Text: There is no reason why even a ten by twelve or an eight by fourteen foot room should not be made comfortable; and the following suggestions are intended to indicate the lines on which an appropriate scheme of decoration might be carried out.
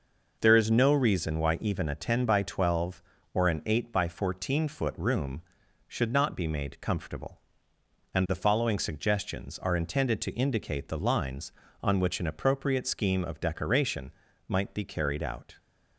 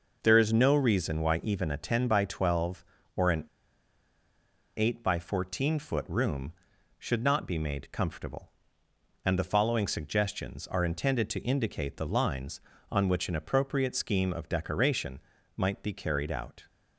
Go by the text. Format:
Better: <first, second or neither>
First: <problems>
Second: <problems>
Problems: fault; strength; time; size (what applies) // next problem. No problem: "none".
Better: first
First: pauses between "decoration" and "might"; slight; at 14.1 s; 0.36 s long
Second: pauses between "an" and "eight"; strong; at 3.4 s; 1.3 s long // pauses between "decoration" and "might"; slight; at 15.2 s; 0.36 s long